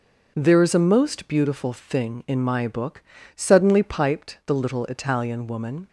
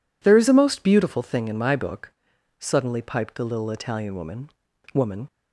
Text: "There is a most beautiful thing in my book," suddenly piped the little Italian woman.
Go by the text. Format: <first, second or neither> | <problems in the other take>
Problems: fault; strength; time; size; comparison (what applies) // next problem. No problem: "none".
first | says "woman" twice; at 4.9 s